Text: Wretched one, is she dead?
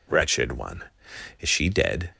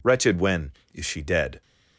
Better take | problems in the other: first | says "when" for "one"; at 0.3 s

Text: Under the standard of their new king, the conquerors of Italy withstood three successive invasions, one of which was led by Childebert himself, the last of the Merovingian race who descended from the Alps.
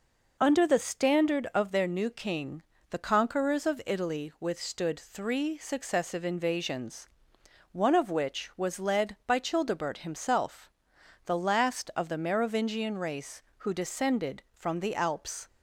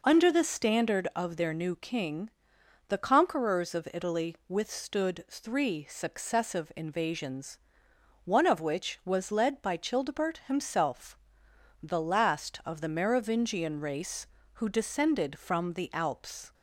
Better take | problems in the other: neither | none

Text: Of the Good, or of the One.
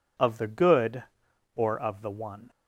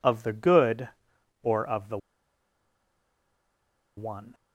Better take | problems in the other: first | pauses between "the" and "One"; strong; at 1.9 s; 2.0 s long

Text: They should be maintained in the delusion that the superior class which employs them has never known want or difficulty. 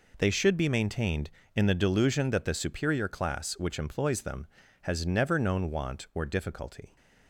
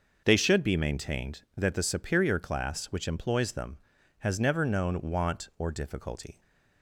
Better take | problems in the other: first | starts louder than the rest; noticeable; until 1.2 s; 6 dB // skips "in the delusion"; at 1.4 s

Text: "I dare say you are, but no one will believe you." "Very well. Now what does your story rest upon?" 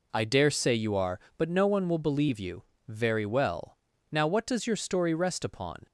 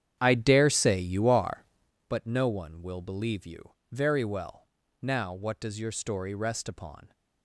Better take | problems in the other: first | starts louder than the rest; strong; until 2.0 s; 9 dB

